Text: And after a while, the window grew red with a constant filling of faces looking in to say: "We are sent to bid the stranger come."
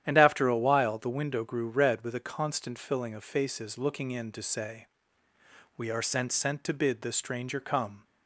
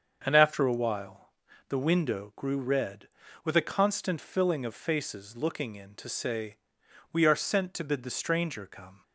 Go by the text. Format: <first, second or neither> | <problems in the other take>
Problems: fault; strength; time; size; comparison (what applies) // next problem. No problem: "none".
second | starts louder than the rest; strong; until 1.0 s; 10.5 dB; also in the second // says "sent" twice; at 6.3 s